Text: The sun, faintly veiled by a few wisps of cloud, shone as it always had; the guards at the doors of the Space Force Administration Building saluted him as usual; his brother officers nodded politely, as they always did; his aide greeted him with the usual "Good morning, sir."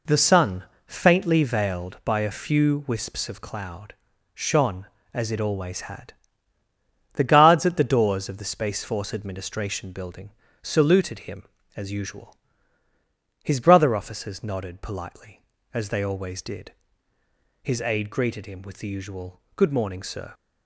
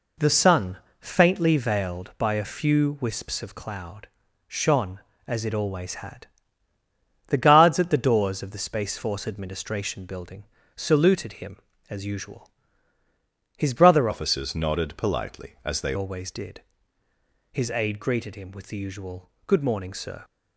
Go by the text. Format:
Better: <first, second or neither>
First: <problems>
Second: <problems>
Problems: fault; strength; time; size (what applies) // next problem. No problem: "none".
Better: first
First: pauses between "Building" and "saluted"; slight; at 10.2 s; 0.32 s long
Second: pauses between "Building" and "saluted"; slight; at 10.4 s; 0.32 s long // changes voice from "officers" to "they"; from 14.1 to 15.9 s; 1.8 s long // pauses between "usual" and "Good"; slight; at 19.3 s; 0.16 s long